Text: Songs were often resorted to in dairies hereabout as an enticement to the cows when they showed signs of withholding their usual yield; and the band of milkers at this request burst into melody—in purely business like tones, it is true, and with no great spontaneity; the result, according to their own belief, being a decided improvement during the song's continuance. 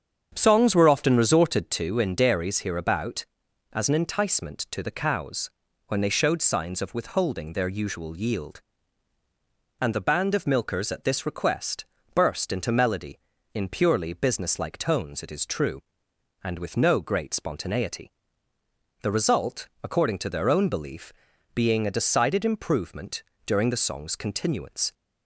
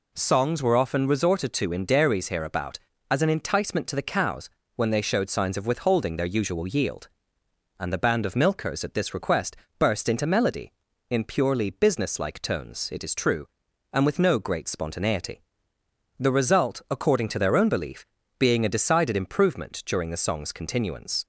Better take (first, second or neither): second